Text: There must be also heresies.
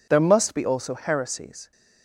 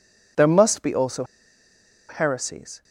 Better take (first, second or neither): first